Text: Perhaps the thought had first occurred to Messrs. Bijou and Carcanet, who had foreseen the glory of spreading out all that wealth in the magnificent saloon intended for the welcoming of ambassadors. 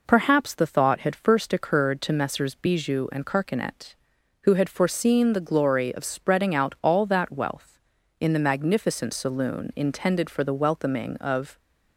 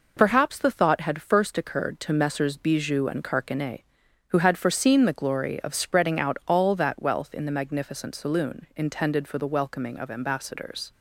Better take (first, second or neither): second